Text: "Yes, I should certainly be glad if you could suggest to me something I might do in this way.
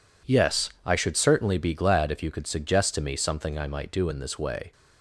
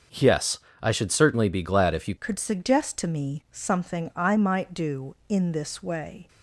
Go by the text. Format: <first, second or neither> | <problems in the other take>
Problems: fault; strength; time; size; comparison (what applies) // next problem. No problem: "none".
first | starts louder than the rest; noticeable; until 1.3 s; 6 dB // changes voice at "could"; from 2.1 s on; 4.1 s long